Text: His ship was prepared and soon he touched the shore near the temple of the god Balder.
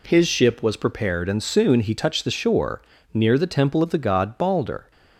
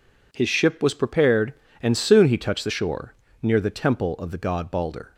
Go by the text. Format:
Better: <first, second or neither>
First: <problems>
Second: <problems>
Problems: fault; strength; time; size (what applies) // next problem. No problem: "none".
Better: neither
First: pauses between "shore" and "near"; slight; at 2.8 s; 0.32 s long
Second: pauses between "shore" and "near"; slight; at 3.1 s; 0.28 s long